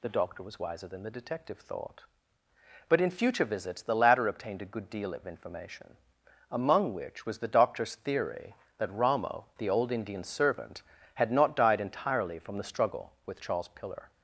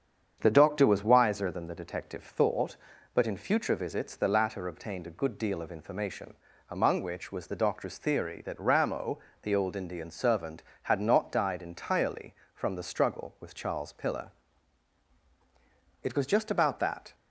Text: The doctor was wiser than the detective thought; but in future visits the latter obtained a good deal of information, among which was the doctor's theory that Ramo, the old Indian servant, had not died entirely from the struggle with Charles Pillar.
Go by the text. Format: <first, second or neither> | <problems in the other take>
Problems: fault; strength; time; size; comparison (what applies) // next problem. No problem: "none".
first | starts louder than the rest; strong; until 1.4 s; 7.5 dB // goes on to say "It was just about that"; noticeable; from 16.0 s on; 1.1 s long